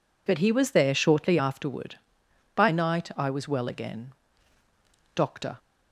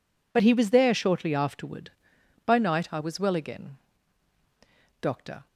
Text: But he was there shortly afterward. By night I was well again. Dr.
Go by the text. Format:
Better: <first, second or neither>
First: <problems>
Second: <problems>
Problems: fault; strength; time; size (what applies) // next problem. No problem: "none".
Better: neither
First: none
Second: none